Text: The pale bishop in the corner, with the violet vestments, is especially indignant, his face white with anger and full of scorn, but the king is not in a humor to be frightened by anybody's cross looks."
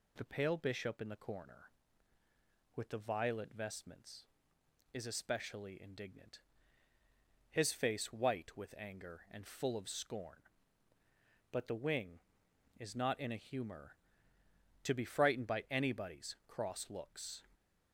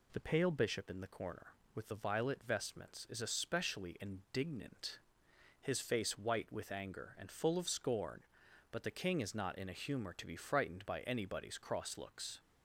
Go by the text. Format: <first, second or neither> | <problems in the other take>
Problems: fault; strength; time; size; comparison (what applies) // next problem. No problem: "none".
second | says "wing" for "king"; at 11.7 s